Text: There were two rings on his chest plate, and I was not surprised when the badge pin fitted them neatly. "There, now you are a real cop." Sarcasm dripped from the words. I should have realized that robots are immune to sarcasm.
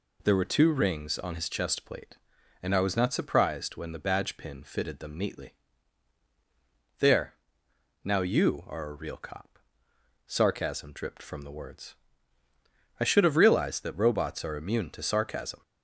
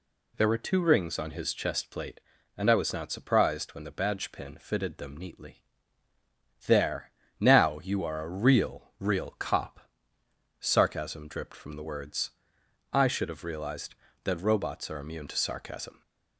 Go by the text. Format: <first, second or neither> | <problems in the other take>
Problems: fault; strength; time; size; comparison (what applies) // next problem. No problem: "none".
first | says "real" twice; at 8.9 s